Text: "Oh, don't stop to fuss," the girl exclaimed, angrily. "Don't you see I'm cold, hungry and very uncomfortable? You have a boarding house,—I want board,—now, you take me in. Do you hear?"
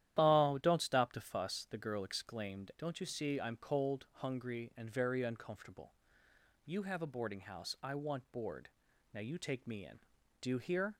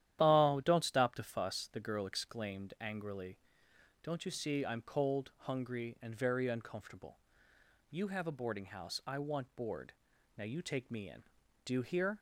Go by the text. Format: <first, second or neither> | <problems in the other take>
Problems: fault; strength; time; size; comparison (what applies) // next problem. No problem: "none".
second | starts louder than the rest; strong; until 1.2 s; 11.5 dB; strong in the second // skips "angrily"; at 2.7 s